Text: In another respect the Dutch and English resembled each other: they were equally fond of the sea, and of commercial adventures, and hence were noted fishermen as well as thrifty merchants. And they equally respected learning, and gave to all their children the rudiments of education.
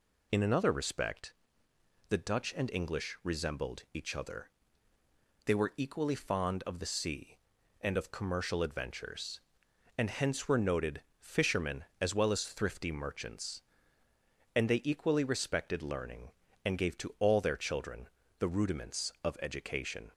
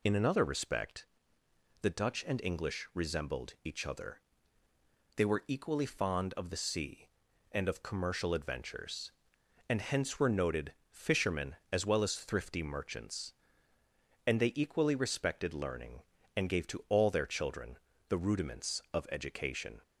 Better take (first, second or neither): neither